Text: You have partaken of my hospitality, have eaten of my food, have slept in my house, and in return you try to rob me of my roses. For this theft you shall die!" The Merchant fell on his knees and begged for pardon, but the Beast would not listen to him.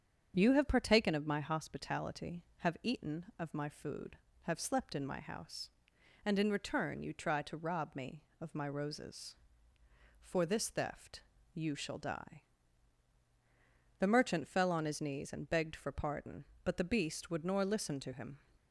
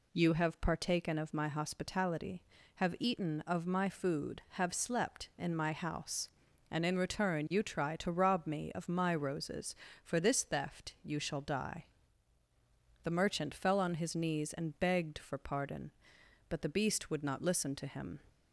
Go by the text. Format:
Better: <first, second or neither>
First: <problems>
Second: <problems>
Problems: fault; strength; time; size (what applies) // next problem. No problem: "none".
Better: second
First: starts louder than the rest; strong; until 1.4 s; 7.5 dB // pauses between "theft" and "you"; slight; at 11.2 s; 0.32 s long // says "nor" for "not"; at 17.4 s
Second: none